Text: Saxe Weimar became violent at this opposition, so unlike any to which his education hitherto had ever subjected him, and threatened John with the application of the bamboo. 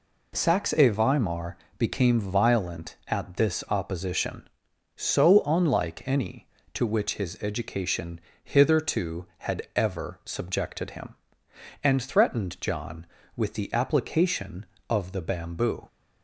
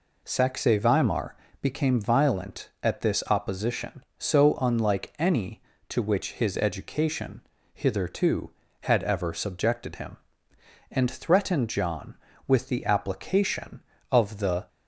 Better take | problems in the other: first | pauses between "Weimar" and "became"; slight; at 1.3 s; 0.24 s long; slight in the first // pauses between "education" and "hitherto"; slight; at 7.4 s; 0.32 s long; slight in the first // stops before "bamboo"; at 14.6 s

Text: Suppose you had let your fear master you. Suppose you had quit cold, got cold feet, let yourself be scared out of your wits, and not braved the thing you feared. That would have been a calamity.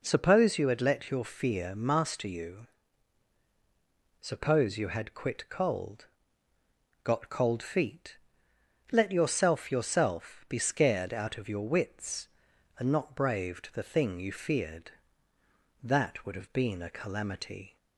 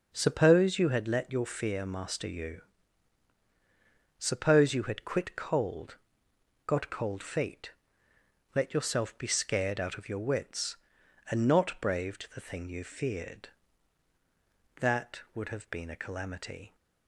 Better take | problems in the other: second | says "yourself" twice; at 9.7 s

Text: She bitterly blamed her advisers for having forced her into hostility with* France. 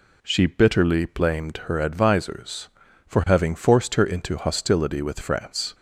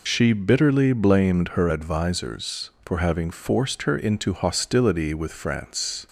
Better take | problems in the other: first | loses the start of "She"; at 0.0 s; 35 ms

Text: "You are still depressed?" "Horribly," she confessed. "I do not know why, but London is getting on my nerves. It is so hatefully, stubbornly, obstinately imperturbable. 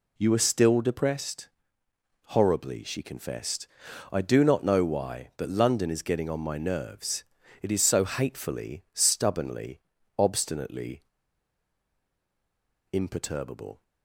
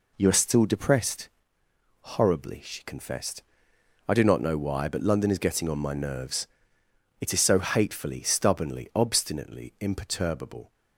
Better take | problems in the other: second | pauses between "obstinately" and "imperturbable"; strong; at 11.0 s; 1.9 s long

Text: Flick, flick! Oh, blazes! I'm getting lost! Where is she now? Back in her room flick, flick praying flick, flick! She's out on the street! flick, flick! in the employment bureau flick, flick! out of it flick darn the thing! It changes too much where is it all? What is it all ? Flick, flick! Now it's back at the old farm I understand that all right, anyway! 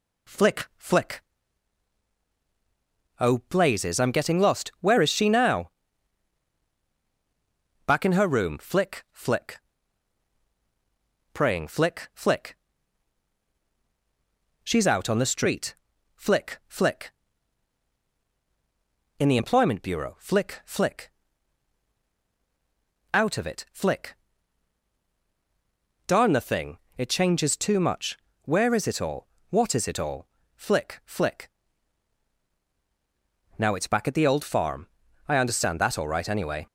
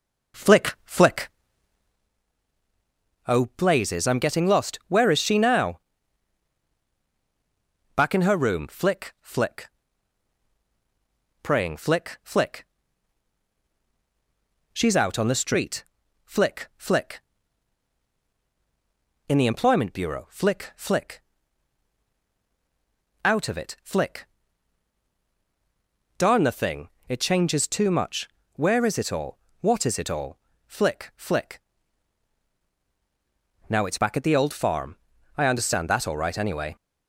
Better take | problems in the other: first | starts louder than the rest; noticeable; until 2.1 s; 5.5 dB // pauses between "flick" and "praying"; strong; at 9.6 s; 1.7 s long; strong in the first // pauses between "flick" and "darn"; strong; at 24.2 s; 1.9 s long; strong in the first // pauses between "much" and "where"; slight; at 28.2 s; 0.30 s long; slight in the first // pauses between "farm" and "I"; at 34.9 s; 0.42 s long; also in the first

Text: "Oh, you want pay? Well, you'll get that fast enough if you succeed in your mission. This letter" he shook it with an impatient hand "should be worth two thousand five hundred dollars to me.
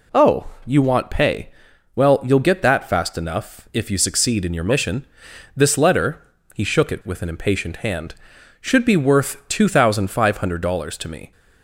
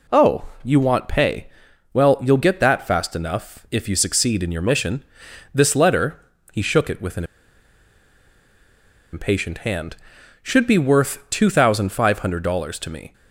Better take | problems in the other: first | pauses between "letter" and "he"; slight; at 6.2 s; 0.32 s long; slight in the first // pauses between "an" and "impatient"; strong; at 7.2 s; 1.8 s long

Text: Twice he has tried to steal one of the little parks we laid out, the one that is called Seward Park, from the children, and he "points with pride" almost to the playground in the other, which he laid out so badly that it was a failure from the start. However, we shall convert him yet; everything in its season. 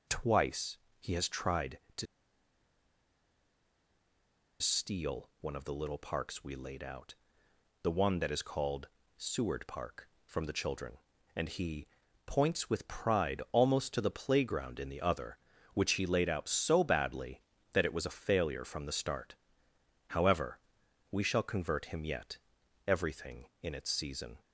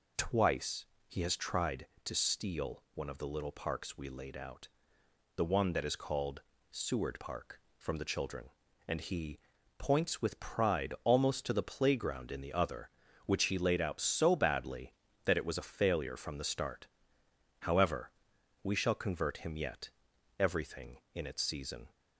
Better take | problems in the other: second | pauses between "Twice" and "he"; slight; at 0.7 s; 0.22 s long; slight in the second // pauses between "to" and "steal"; strong; at 2.0 s; 2.5 s long // pauses between "called" and "Seward"; slight; at 8.8 s; 0.30 s long; slight in the second // pauses between "he" and "points"; at 11.8 s; 0.38 s long; also in the second

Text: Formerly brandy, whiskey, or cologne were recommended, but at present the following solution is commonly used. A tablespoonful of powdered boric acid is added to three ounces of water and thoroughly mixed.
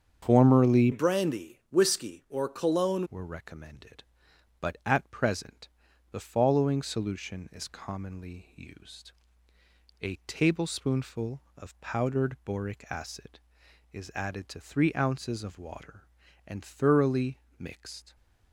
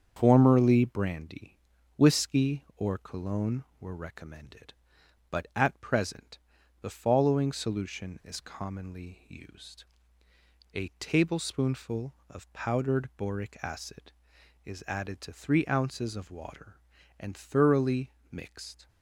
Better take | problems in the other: second | starts louder than the rest; strong; until 1.2 s; 7.5 dB; strong in the second // changes voice from "brandy" to "cologne"; from 0.9 to 3.0 s; 2.1 s long // pauses between "present" and "the"; at 5.6 s; 0.42 s long; also in the second // pauses between "thoroughly" and "mixed"; slight; at 17.3 s; 0.18 s long; slight in the second

